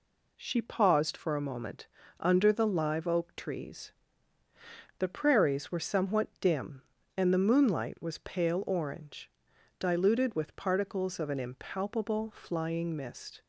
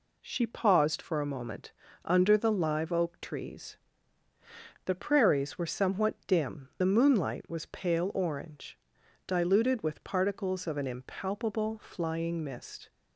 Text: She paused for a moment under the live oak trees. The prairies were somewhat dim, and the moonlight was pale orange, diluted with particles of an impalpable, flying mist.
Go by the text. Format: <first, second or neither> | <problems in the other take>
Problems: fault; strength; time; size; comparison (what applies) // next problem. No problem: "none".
first | pauses between "moment" and "under"; slight; at 1.7 s; 0.32 s long; slight in the first // skips "and"; at 6.7 s